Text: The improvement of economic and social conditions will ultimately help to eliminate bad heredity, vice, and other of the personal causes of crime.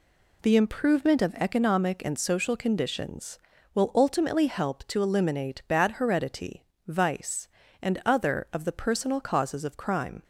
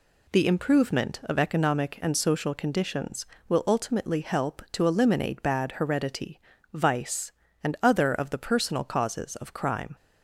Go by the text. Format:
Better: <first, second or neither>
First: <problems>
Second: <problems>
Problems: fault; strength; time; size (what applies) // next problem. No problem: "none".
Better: neither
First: none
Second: none